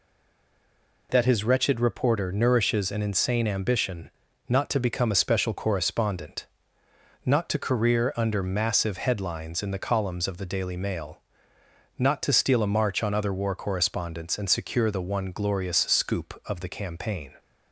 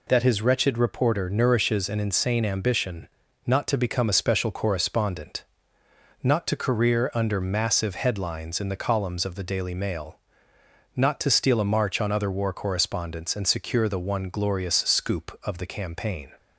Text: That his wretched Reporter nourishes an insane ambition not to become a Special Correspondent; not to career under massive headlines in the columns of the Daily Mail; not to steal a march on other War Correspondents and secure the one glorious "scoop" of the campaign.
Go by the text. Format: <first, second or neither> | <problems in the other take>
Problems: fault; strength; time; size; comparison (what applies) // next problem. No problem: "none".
second | stays silent before the first word; until 1.0 s; 1.0 s long // pauses between "ambition" and "not"; at 4.1 s; 0.38 s long; also in the second